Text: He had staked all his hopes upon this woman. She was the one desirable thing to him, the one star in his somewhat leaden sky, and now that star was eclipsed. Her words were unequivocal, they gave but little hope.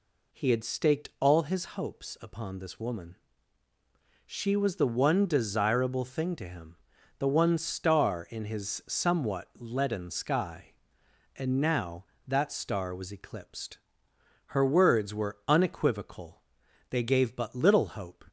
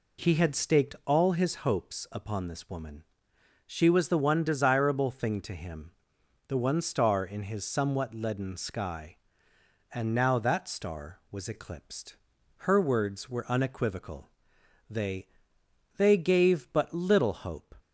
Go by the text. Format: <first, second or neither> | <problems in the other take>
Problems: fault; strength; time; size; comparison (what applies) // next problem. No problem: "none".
first | says "they" twice; at 15.9 s